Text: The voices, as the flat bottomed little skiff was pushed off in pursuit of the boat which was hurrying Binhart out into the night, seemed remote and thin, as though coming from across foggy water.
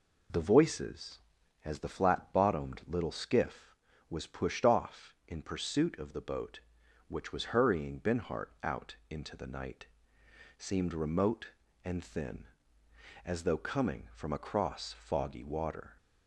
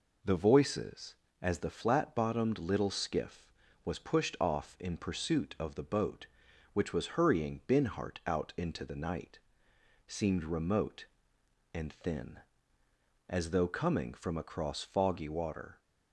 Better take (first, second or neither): neither